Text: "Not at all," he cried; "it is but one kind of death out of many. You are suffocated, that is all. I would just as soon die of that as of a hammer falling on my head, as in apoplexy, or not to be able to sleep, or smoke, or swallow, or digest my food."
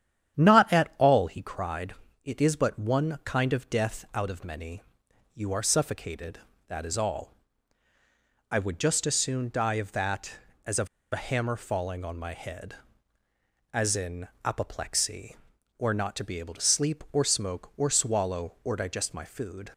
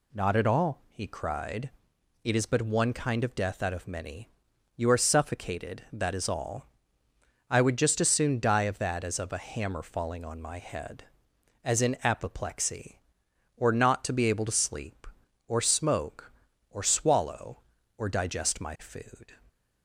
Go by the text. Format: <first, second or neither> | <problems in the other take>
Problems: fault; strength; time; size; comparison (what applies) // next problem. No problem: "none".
second | starts louder than the rest; strong; until 1.4 s; 10 dB // pauses between "of" and "a"; slight; at 10.8 s; 0.24 s long // pauses between "in" and "apoplexy"; slight; at 14.2 s; 0.18 s long